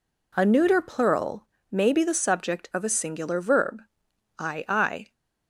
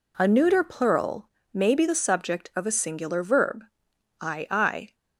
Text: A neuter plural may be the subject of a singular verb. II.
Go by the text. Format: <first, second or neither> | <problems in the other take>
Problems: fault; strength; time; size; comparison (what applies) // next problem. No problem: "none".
neither | pauses between "plural" and "may"; slight; the same in both